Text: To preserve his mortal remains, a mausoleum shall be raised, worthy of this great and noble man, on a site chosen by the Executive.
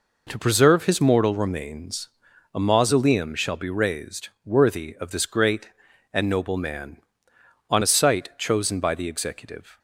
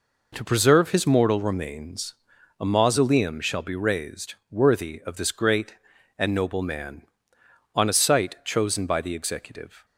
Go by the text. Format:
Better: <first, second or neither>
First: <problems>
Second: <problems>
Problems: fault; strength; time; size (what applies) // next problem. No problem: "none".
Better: neither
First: none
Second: none